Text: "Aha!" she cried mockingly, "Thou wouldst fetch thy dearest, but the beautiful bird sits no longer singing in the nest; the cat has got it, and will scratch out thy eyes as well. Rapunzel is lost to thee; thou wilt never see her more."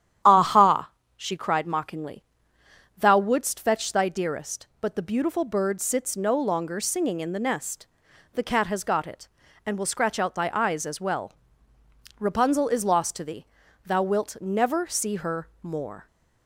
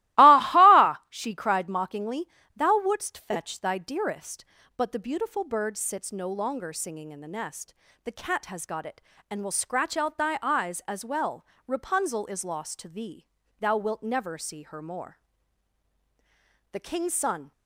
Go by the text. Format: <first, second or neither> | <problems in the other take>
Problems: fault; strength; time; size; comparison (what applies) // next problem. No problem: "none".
first | starts louder than the rest; strong; until 1.2 s; 18 dB; strong in the first // goes on to say "The King's son"; noticeable; from 16.7 s on; 0.80 s long